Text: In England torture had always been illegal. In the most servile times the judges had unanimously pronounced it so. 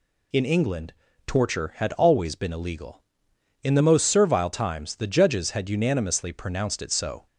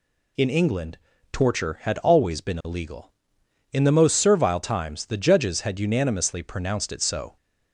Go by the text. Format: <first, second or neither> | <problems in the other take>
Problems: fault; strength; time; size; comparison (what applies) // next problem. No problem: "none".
neither | pauses between "England" and "torture"; slight; the same in both